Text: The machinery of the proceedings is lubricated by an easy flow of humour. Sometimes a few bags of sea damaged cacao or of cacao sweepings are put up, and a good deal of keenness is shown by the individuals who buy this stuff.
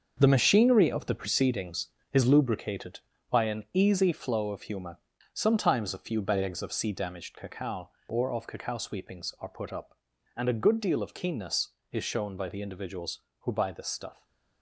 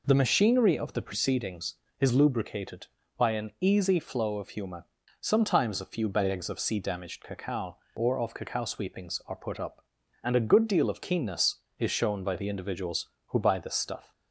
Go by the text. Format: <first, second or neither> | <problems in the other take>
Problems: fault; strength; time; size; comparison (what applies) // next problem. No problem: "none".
second | gets quieter; strong; throughout; 9.5 dB